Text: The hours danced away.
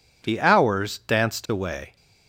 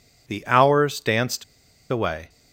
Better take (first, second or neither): first